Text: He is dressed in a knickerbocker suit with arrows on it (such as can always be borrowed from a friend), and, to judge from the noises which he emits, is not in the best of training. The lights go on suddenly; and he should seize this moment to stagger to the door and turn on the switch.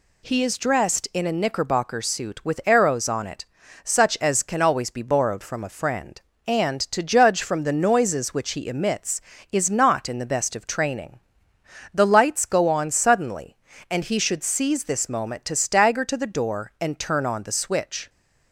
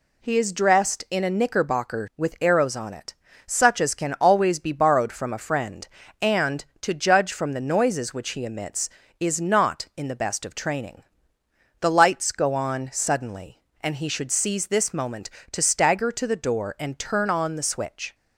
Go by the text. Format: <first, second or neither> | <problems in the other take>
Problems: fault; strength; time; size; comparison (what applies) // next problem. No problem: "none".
first | skips "suit"; at 2.1 s